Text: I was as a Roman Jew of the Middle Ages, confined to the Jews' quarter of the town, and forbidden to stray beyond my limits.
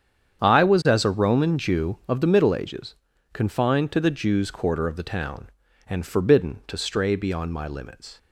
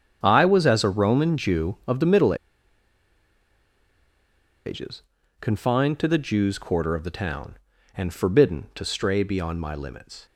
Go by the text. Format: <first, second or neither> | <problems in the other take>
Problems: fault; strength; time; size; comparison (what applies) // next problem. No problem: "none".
first | starts louder than the rest; strong; until 1.2 s; 8.5 dB; strong in the first // pauses between "Middle" and "Ages"; strong; at 2.3 s; 2.3 s long